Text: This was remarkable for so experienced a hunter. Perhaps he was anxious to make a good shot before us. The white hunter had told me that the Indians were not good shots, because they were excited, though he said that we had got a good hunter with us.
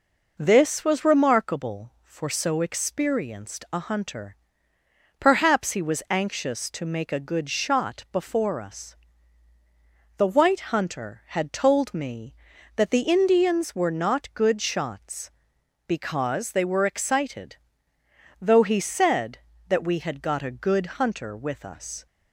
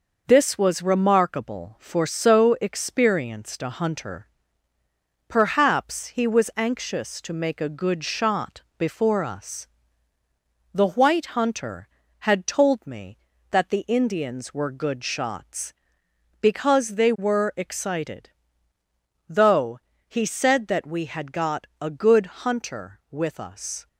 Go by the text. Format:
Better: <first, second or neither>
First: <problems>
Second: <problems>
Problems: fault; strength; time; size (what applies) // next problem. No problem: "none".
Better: first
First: none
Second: pauses between "shot" and "before"; slight; at 8.6 s; 0.16 s long // skips "not"; at 14.7 s // pauses between "though" and "he"; slight; at 19.7 s; 0.30 s long // pauses between "good" and "hunter"; slight; at 22.2 s; 0.18 s long